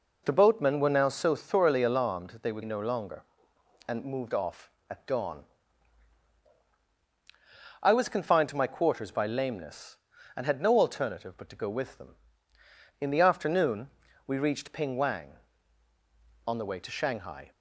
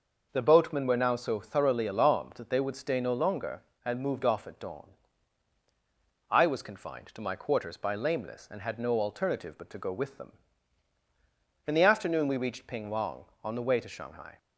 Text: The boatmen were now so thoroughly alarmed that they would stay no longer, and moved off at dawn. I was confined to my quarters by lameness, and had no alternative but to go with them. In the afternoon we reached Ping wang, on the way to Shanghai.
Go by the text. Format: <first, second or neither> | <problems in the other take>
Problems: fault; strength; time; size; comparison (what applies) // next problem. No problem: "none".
second | skips "stay"; at 2.6 s // pauses between "afternoon" and "we"; at 13.8 s; 0.38 s long